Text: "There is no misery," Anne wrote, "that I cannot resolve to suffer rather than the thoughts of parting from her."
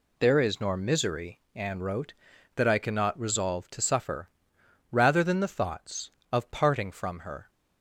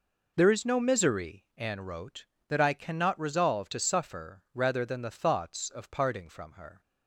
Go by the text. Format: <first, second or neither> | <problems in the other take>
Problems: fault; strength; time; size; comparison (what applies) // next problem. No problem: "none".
second | says "nor" for "no"; at 0.6 s // pauses between "suffer" and "rather"; noticeable; at 4.2 s; 0.60 s long